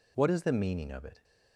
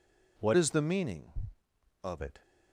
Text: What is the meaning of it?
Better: first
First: none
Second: changes voice from "is" to "of"; from 0.5 to 2.2 s; 1.7 s long

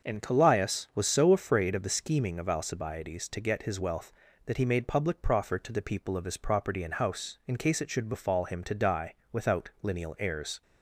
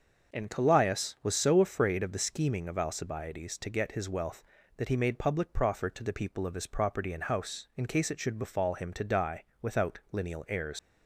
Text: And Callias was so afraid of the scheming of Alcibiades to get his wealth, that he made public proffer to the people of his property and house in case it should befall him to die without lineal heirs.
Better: first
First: starts louder than the rest; until 1.1 s; 6.5 dB // pauses between "die" and "without"; slight; at 9.1 s; 0.18 s long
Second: starts louder than the rest; until 1.3 s; 6.5 dB // pauses between "die" and "without"; slight; at 9.4 s; 0.18 s long // leaves "heirs" unfinished; at 10.7 s; 120 ms

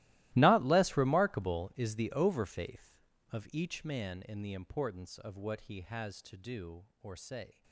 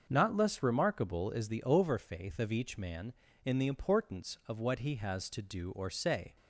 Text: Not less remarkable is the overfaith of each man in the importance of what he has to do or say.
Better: second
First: gets quieter; strong; throughout; 20 dB // starts louder than the rest; strong; until 1.3 s; 17 dB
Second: starts louder than the rest; until 1.1 s; 6.5 dB

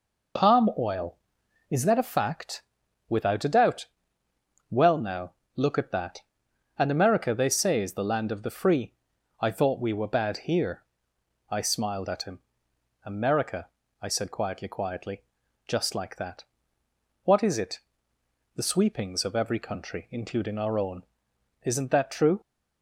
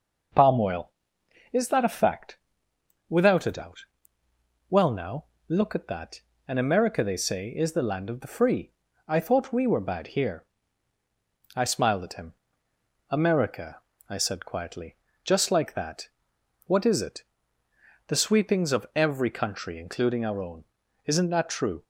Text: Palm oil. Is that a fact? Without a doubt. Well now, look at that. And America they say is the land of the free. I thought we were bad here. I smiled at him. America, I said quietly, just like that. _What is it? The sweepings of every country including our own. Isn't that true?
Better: second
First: says "quietly" twice; at 14.6 s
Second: none

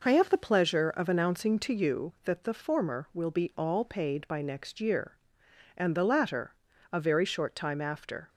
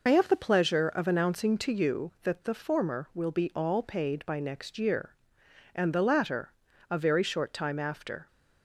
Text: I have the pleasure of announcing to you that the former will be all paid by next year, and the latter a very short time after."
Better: first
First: pauses between "latter" and "a"; at 6.5 s; 0.40 s long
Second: loses the start of "I"; at 0.0 s; 60 ms // pauses between "latter" and "a"; at 6.5 s; 0.40 s long

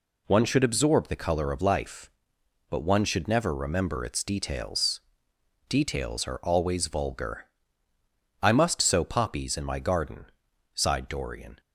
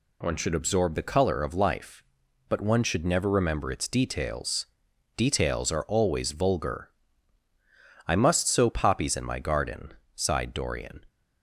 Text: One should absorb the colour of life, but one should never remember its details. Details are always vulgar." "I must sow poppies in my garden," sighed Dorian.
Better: neither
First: none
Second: none

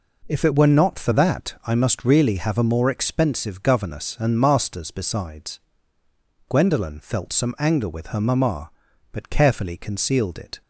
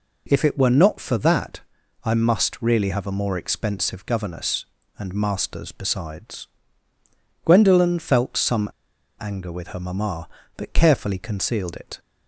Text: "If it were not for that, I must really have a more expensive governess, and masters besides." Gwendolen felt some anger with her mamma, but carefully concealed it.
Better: first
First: none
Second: pauses between "some" and "anger"; noticeable; at 8.6 s; 0.52 s long

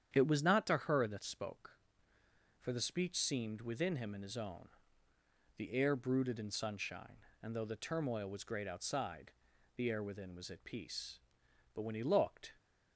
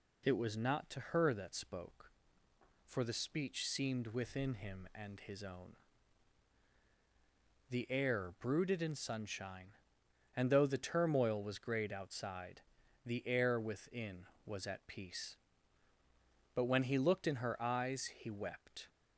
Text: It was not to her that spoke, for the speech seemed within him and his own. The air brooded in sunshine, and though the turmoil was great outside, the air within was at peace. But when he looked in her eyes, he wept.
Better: second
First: starts louder than the rest; strong; until 1.1 s; 9 dB // stops before "in her eyes he wept"; at 12.5 s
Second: none

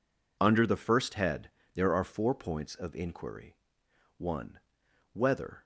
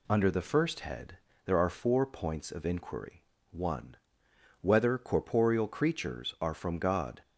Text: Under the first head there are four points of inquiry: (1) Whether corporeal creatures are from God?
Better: second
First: pauses between "head" and "there"; slight; at 1.4 s; 0.24 s long // stops before "corporeal creatures are from God"; at 5.6 s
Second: pauses between "head" and "there"; slight; at 1.1 s; 0.28 s long

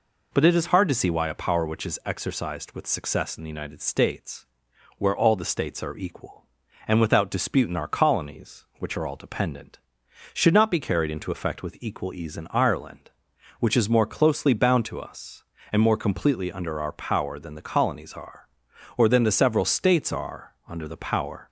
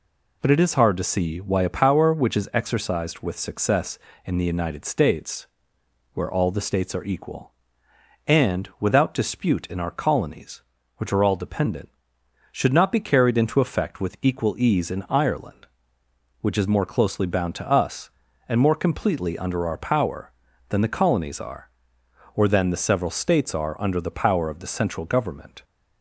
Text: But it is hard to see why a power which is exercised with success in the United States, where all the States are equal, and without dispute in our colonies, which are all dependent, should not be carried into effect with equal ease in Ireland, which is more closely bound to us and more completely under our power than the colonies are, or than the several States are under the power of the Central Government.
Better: second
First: stops before "of the Central Government"; at 21.4 s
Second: none

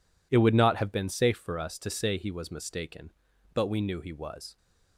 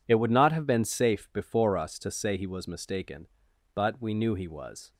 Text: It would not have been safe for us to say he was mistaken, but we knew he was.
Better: first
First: none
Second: says "before" for "for"; at 1.3 s

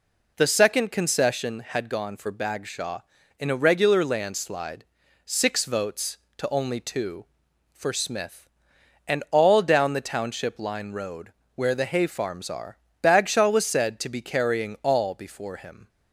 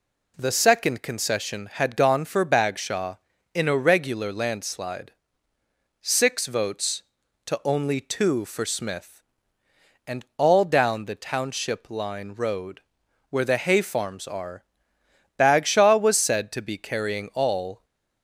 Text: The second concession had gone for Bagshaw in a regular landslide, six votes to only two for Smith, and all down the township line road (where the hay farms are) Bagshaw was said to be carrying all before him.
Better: first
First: none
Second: stops before "before him"; at 17.8 s

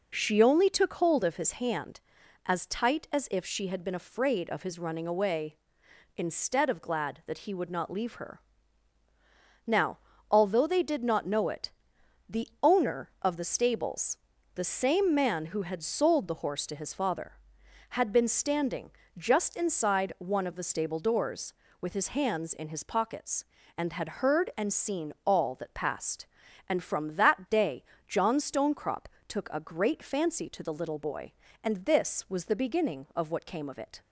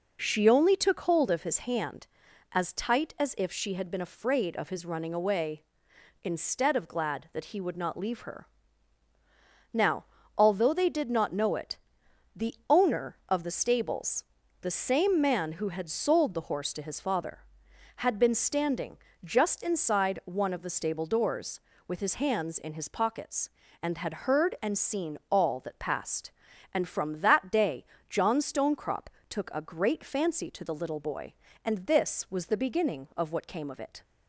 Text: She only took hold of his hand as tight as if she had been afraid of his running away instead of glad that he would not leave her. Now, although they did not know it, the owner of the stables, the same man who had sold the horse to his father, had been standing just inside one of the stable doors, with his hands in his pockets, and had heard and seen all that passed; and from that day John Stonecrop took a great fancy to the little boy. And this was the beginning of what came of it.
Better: neither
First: pauses between "standing" and "just"; slight; at 18.9 s; 0.26 s long // pauses between "day" and "John"; slight; at 27.8 s; 0.24 s long // pauses between "Stonecrop" and "took"; slight; at 29.0 s; 0.22 s long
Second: pauses between "standing" and "just"; slight; at 18.9 s; 0.26 s long // pauses between "day" and "John"; slight; at 27.8 s; 0.24 s long // pauses between "Stonecrop" and "took"; slight; at 29.0 s; 0.22 s long

